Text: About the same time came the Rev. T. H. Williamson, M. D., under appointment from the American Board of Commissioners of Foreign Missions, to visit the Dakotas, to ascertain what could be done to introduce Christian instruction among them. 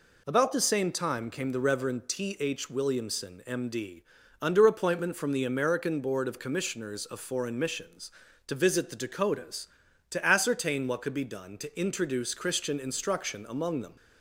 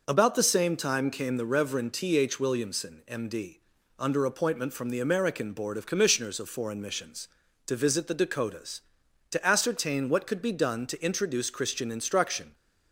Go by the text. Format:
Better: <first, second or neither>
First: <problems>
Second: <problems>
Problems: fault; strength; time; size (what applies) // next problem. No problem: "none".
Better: first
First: none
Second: stops before "among them"; at 12.5 s